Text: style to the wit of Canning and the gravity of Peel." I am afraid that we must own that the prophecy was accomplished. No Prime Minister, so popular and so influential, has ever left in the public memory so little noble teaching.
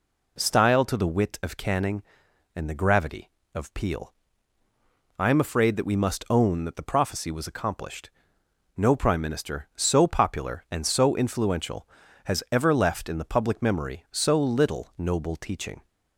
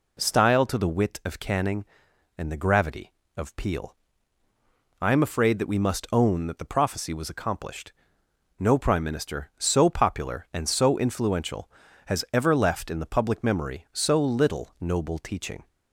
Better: neither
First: none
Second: none

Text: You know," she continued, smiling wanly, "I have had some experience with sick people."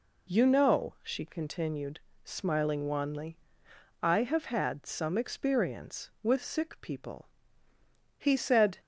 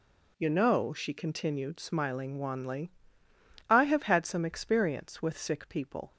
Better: second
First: goes on to say "He said"; noticeable; from 8.1 s on; 0.62 s long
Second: none

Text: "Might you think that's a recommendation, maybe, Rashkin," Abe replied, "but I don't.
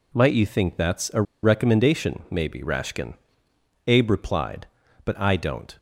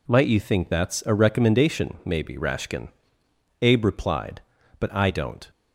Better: second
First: pauses between "a" and "recommendation"; slight; at 1.2 s; 0.20 s long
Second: none

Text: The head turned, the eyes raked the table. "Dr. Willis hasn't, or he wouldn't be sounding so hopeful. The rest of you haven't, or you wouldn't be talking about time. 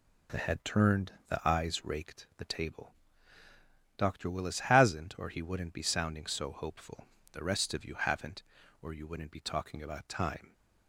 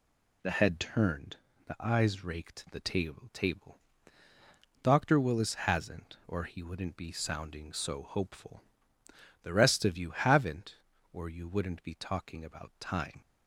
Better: first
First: none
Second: says "table" twice; at 3.3 s

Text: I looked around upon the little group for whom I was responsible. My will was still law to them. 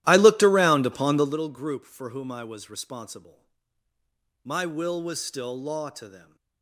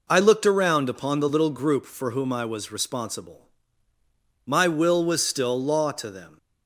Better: second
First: starts louder than the rest; strong; until 1.4 s; 14 dB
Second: none

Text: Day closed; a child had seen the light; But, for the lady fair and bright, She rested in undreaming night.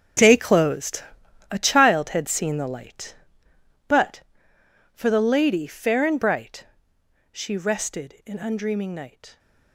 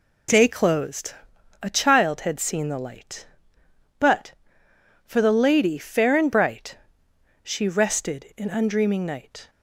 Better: second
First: gets quieter; strong; throughout; 13.5 dB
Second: none

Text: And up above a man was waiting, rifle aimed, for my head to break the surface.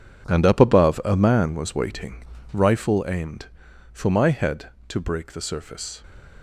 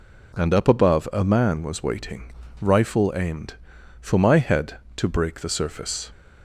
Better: second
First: gets quieter; strong; throughout; 12 dB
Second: none

